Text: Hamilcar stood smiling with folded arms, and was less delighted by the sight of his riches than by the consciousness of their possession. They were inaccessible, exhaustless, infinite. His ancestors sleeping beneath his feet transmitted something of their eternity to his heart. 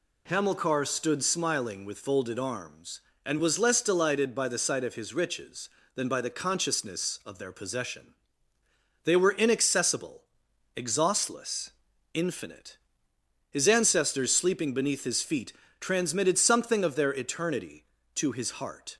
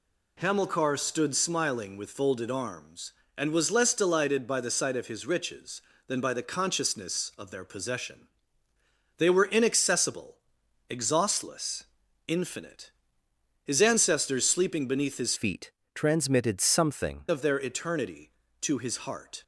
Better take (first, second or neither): first